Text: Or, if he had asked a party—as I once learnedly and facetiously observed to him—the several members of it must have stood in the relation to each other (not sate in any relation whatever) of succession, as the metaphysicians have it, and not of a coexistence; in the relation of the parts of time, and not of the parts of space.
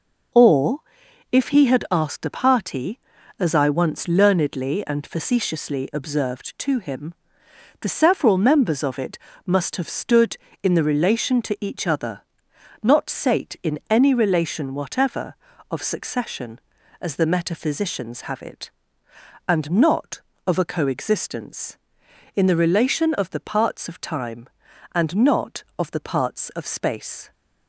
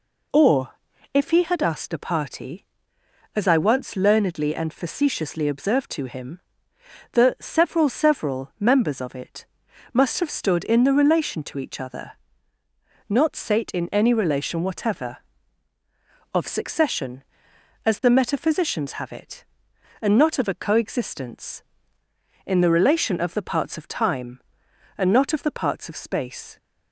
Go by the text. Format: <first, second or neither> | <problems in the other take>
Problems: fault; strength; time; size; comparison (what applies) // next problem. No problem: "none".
first | says "several" twice; at 7.8 s // pauses between "it" and "must"; noticeable; at 9.4 s; 0.48 s long; slight in the first